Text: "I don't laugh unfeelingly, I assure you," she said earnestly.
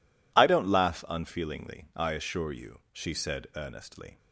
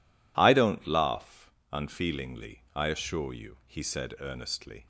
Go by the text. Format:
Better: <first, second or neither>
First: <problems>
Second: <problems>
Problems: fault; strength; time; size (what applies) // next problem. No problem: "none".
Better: first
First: none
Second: pauses between "laugh" and "unfeelingly"; slight; at 1.4 s; 0.22 s long // says "he" for "she"; at 3.6 s